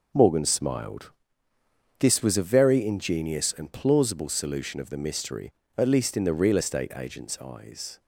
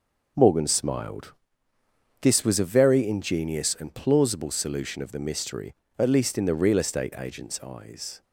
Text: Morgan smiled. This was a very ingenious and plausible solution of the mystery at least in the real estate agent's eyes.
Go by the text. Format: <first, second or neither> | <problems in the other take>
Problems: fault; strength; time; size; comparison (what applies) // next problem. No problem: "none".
neither | none